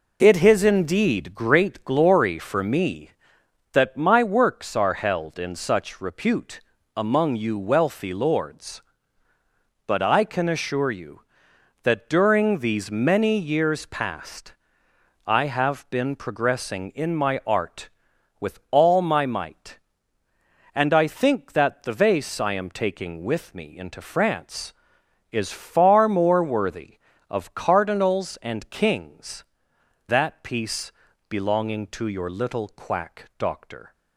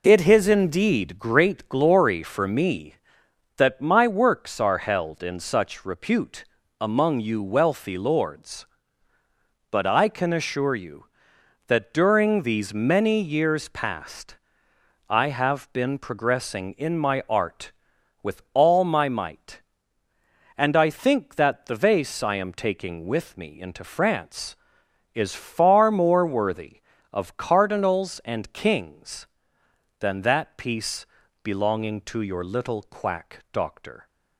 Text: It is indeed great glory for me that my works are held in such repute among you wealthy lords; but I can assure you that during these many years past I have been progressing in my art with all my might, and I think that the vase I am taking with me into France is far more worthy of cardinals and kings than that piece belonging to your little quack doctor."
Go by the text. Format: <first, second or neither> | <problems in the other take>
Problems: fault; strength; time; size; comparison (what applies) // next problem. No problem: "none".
second | pauses between "repute" and "among"; slight; at 6.6 s; 0.34 s long; slight in the second // pauses between "past" and "I"; noticeable; at 14.5 s; 0.72 s long; noticeable in the second // skips "than"; at 29.7 s // pauses between "piece" and "belonging"; at 30.9 s; 0.38 s long; also in the second // pauses between "quack" and "doctor"; slight; at 33.2 s; 0.16 s long; slight in the second